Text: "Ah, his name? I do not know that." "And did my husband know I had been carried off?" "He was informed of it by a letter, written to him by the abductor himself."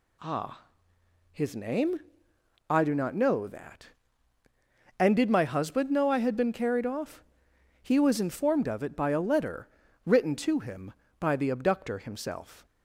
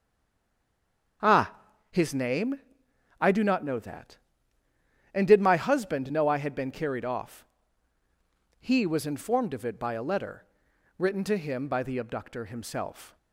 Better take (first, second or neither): first